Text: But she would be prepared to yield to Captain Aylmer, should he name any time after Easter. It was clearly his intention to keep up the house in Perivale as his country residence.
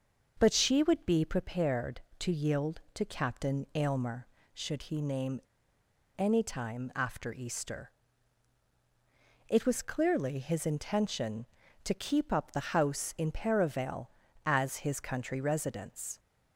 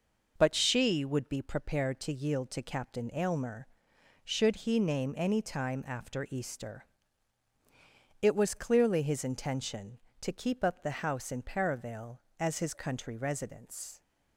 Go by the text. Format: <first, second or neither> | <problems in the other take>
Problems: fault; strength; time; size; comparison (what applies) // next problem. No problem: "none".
second | starts louder than the rest; until 1.3 s; 6 dB // pauses between "name" and "any"; noticeable; at 5.4 s; 0.77 s long